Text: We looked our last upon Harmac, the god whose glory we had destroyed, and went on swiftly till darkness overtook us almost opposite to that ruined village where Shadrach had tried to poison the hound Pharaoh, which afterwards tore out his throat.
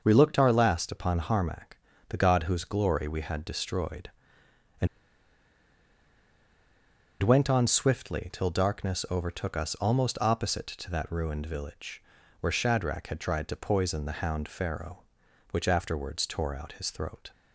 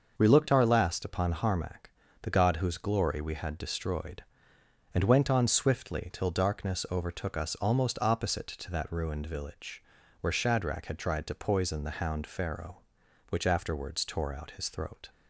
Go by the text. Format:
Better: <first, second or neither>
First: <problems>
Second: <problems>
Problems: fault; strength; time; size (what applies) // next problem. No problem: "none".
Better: second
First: starts louder than the rest; until 1.0 s; 6 dB // pauses between "and" and "went"; strong; at 4.8 s; 2.3 s long // pauses between "village" and "where"; at 12.0 s; 0.38 s long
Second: starts louder than the rest; until 1.2 s; 6 dB // pauses between "village" and "where"; at 9.8 s; 0.38 s long